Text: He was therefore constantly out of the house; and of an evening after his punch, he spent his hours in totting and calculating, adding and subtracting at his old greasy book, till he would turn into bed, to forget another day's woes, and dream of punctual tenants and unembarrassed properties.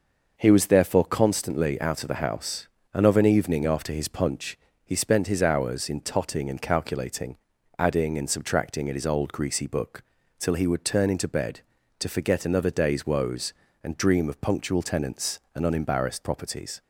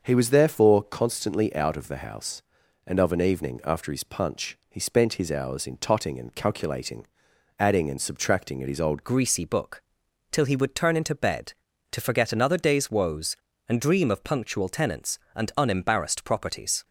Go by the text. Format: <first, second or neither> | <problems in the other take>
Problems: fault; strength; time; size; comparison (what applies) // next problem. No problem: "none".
first | starts louder than the rest; until 1.0 s; 6 dB // changes voice at "greasy"; from 9.0 s on; 7.8 s long